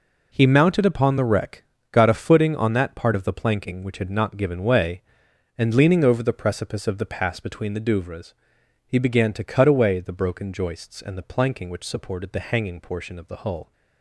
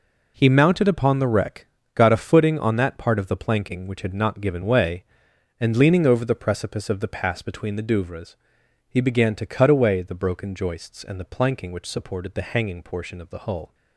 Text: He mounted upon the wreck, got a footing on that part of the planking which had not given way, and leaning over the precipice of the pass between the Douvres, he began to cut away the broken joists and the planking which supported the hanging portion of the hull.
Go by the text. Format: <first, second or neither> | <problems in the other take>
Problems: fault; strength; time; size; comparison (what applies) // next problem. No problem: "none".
neither | none